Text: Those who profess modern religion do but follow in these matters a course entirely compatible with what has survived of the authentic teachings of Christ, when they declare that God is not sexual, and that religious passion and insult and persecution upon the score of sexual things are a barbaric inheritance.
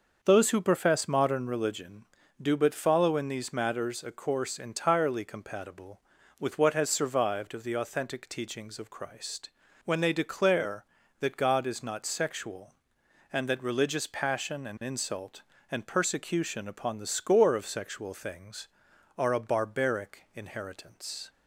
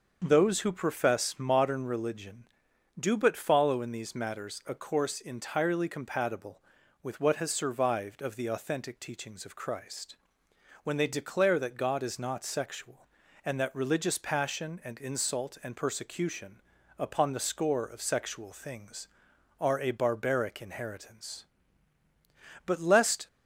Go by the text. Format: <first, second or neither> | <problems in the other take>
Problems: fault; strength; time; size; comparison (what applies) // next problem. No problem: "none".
first | starts louder than the rest; until 1.2 s; 6.5 dB; also in the first // pauses between "persecution" and "upon"; at 16.6 s; 0.38 s long // goes on to say "But lest"; from 22.6 s on; 0.60 s long